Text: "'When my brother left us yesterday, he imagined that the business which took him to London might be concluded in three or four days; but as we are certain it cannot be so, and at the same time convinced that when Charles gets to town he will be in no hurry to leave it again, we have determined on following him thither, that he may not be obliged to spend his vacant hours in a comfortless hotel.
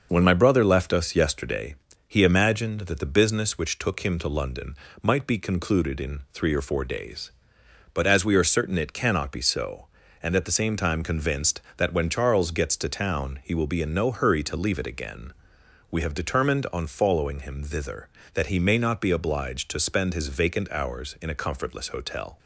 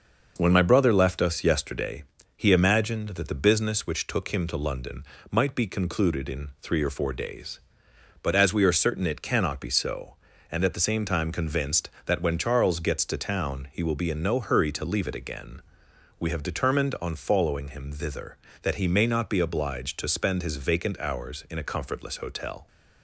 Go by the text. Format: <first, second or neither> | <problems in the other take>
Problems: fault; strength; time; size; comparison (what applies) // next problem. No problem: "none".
second | loses the start of "When"; at 0.0 s; 20 ms // starts louder than the rest; noticeable; until 1.1 s; 6 dB; noticeable in the second // pauses between "London" and "might"; slight; at 4.7 s; 0.28 s long; slight in the second